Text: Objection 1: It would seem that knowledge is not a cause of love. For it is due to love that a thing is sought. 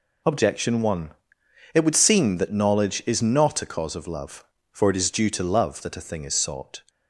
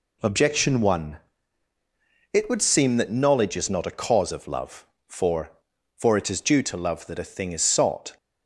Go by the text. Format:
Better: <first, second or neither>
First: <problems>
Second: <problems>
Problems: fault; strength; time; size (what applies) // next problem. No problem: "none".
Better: first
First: none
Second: says "For" twice; at 5.9 s